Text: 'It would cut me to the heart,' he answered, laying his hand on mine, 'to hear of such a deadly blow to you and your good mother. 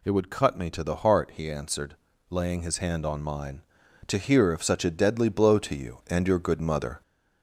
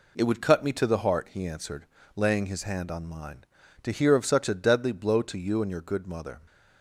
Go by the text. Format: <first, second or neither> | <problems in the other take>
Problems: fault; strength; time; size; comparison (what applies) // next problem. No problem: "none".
second | gets louder; slight; throughout; 2 dB